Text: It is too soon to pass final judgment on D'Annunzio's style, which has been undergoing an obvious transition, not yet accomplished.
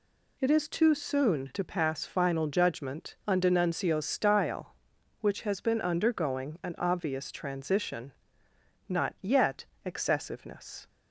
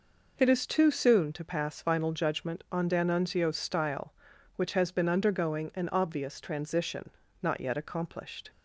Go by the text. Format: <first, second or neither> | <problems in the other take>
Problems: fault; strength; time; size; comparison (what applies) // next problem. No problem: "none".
second | says "excessiveness" for "accomplished"; at 9.8 s